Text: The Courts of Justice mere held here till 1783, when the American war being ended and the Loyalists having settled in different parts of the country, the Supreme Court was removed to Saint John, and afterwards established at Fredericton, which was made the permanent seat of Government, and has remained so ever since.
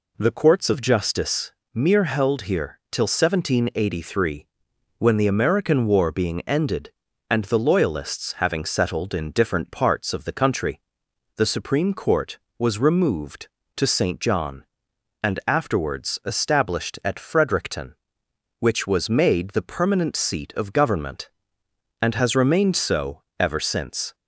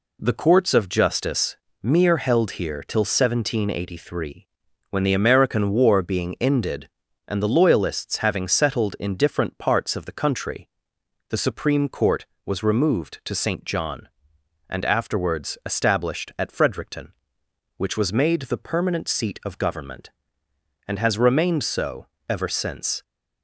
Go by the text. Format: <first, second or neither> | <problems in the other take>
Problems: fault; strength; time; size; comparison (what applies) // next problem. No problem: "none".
neither | pauses between "Justice" and "mere"; slight; the same in both // pauses between "so" and "ever"; slight; the same in both